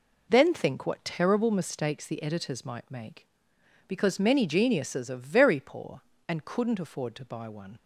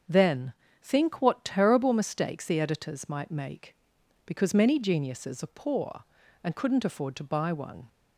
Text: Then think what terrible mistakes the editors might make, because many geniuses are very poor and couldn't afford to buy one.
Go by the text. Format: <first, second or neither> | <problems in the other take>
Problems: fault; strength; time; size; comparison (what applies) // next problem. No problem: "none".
first | starts louder than the rest; strong; until 1.3 s; 7 dB // pauses between "Then" and "think"; slight; at 0.5 s; 0.30 s long // skips "very"; at 5.5 s